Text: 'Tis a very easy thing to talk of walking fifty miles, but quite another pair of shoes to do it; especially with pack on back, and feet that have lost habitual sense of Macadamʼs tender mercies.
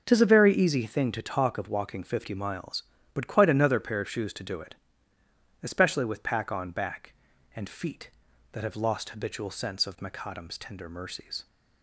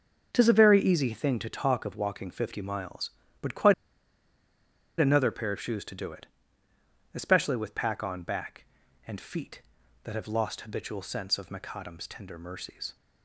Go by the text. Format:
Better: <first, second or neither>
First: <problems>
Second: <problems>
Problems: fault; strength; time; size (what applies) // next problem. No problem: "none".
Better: first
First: none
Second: pauses between "quite" and "another"; strong; at 3.7 s; 1.2 s long